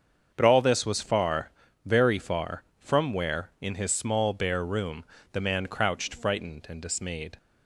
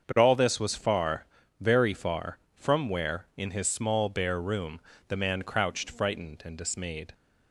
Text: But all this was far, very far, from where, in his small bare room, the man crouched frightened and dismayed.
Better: neither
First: starts louder than the rest; until 1.3 s; 7 dB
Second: starts louder than the rest; until 1.1 s; 6.5 dB

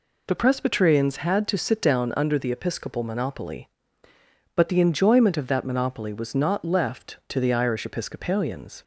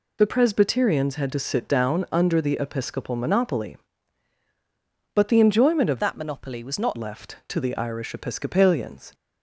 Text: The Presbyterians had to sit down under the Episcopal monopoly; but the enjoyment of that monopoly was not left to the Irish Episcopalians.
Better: first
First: none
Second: changes voice from "that" to "not"; from 5.9 to 6.9 s; 1.0 s long

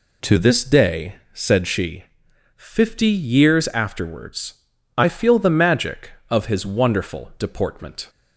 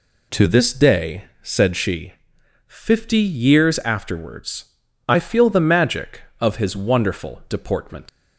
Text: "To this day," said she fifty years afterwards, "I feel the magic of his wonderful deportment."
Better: first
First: pauses between "she" and "fifty"; noticeable; at 2.0 s; 0.52 s long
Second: pauses between "she" and "fifty"; noticeable; at 2.1 s; 0.54 s long // leaves "deportment" unfinished; at 8.0 s; 105 ms

